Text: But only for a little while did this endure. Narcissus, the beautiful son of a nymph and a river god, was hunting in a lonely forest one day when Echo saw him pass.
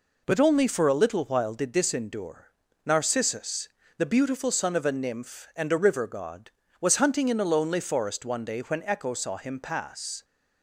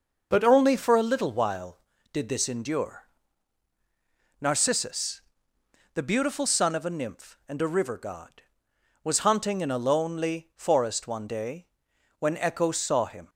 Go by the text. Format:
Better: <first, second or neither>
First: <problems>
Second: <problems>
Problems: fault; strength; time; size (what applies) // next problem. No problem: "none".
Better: first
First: none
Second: pauses between "day" and "when"; noticeable; at 11.6 s; 0.56 s long // stops before "pass"; at 13.2 s